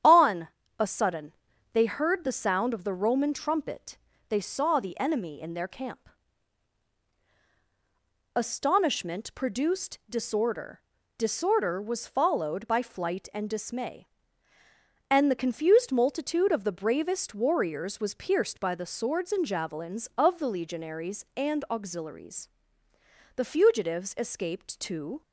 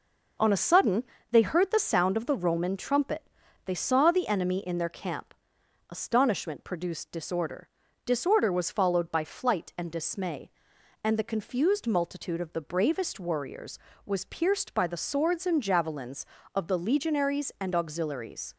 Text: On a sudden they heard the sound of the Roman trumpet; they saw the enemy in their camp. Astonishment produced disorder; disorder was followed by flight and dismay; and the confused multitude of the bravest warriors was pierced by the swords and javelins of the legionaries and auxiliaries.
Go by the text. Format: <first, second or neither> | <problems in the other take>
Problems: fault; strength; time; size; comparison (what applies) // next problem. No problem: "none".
second | starts louder than the rest; strong; until 1.7 s; 9 dB // pauses between "On" and "a"; slight; at 0.4 s; 0.30 s long // pauses between "sudden" and "they"; at 1.3 s; 0.40 s long; slight in the second // goes on to say "The fugitives escaped to"; strong; from 23.3 s on; 1.8 s long